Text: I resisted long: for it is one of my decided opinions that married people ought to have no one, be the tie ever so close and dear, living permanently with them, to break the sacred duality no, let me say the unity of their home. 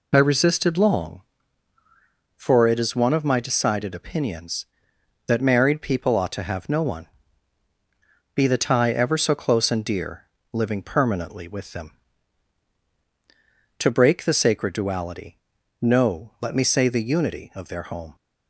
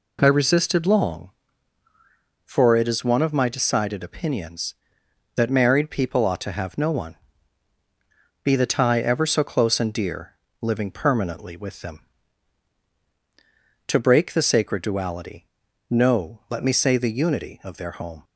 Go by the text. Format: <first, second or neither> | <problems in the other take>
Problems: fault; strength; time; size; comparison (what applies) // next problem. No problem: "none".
second | loses the start of "I"; at 0.1 s; 30 ms // pauses between "duality" and "no"; noticeable; at 15.3 s; 0.46 s long; noticeable in the second